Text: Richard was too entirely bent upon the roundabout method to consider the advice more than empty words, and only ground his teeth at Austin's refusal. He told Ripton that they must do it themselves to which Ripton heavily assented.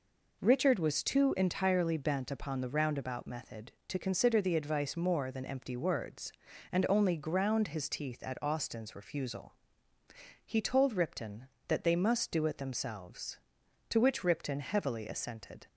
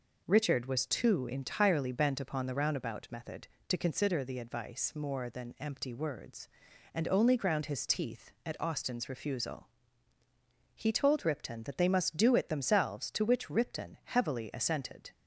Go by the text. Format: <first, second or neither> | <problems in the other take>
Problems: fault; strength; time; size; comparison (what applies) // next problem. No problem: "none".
neither | none